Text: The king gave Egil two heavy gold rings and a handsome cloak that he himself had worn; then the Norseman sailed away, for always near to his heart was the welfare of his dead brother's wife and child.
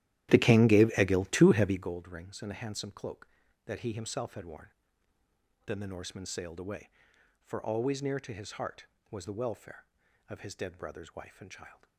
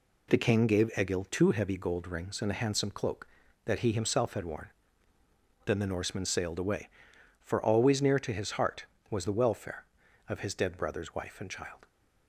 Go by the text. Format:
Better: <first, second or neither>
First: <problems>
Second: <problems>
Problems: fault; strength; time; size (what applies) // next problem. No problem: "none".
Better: second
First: starts louder than the rest; strong; until 2.0 s; 13 dB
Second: none